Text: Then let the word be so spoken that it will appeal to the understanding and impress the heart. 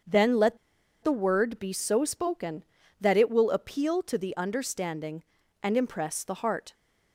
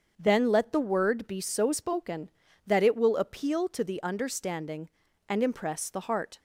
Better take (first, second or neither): second